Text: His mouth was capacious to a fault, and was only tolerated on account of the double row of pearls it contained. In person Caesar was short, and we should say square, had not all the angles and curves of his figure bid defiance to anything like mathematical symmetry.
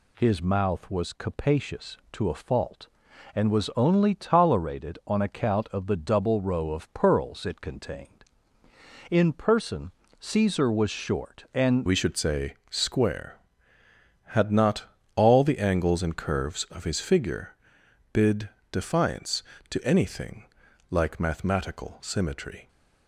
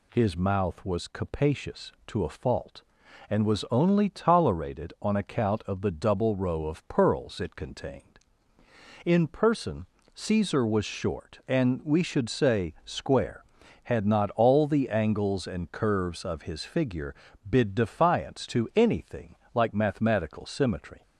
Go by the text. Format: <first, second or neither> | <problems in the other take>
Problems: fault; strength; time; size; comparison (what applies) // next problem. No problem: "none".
second | pauses between "person" and "Caesar"; slight; at 9.9 s; 0.28 s long; slight in the second // changes voice at "we"; from 11.8 s on; 10.8 s long // pauses between "not" and "all"; slight; at 14.8 s; 0.30 s long // pauses between "figure" and "bid"; noticeable; at 17.5 s; 0.58 s long; slight in the second // pauses between "bid" and "defiance"; slight; at 18.4 s; 0.22 s long // pauses between "anything" and "like"; at 20.4 s; 0.44 s long; slight in the second